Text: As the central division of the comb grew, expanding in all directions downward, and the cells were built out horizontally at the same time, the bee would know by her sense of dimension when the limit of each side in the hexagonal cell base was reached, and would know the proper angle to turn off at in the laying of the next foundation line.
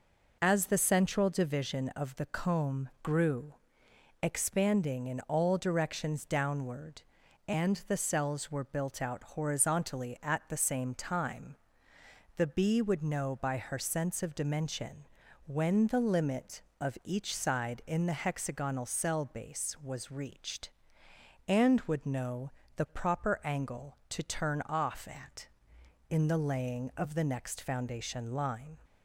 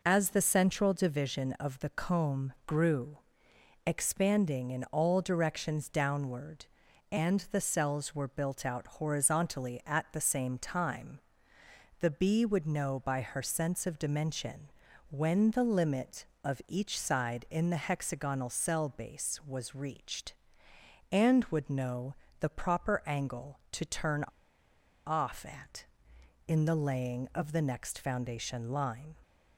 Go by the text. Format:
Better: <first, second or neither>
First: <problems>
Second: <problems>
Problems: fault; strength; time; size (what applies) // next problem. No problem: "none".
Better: first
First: pauses between "dimension" and "when"; at 15.0 s; 0.38 s long // pauses between "know" and "the"; slight; at 22.5 s; 0.26 s long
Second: pauses between "dimension" and "when"; at 14.7 s; 0.38 s long // pauses between "know" and "the"; slight; at 22.1 s; 0.26 s long // pauses between "turn" and "off"; noticeable; at 24.2 s; 0.81 s long